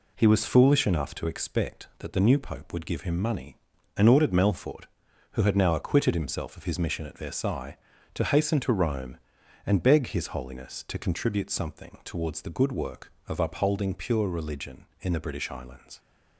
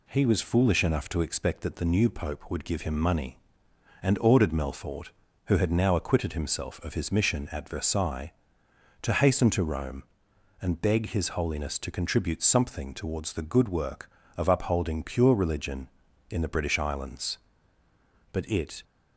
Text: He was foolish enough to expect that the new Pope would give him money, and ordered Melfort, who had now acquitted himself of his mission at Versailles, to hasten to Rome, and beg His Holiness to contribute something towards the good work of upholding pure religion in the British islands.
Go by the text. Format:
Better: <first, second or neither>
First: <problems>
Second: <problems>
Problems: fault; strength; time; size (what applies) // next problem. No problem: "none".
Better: first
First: none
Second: goes on to say "But it"; from 18.3 s on; 0.52 s long